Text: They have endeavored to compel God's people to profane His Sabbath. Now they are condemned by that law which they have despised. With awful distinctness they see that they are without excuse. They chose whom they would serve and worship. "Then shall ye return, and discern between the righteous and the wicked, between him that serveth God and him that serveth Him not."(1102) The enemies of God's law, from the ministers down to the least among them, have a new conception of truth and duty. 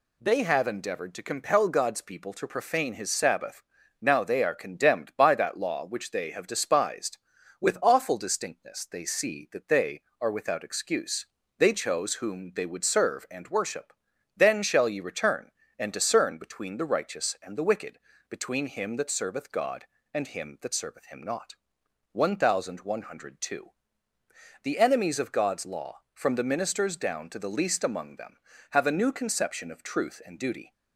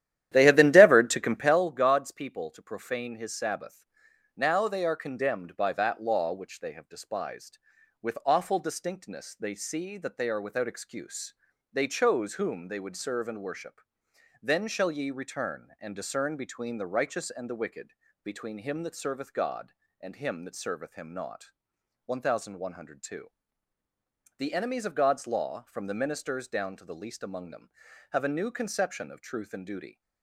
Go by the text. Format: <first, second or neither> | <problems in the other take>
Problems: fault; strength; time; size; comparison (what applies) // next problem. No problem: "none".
first | starts louder than the rest; strong; until 1.6 s; 12 dB